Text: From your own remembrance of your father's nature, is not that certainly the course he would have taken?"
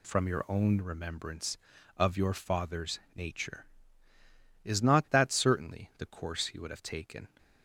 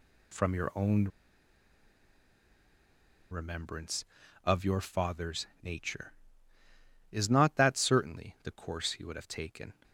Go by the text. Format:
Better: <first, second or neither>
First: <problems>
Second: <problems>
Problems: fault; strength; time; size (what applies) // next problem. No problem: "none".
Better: first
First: pauses between "father's" and "nature"; slight; at 2.9 s; 0.16 s long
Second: pauses between "own" and "remembrance"; strong; at 1.0 s; 2.2 s long // pauses between "father's" and "nature"; slight; at 5.4 s; 0.16 s long